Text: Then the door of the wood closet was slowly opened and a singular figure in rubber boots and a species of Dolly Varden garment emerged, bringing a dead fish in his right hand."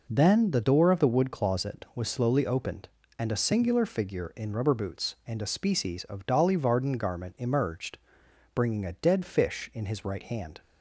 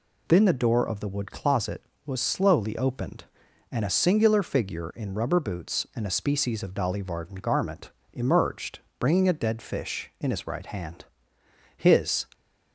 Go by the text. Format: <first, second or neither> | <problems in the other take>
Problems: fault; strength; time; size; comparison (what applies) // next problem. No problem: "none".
first | pauses between "garment" and "emerged"; slight; at 7.9 s; 0.22 s long // goes on to say "HIS"; from 11.7 s on; 0.50 s long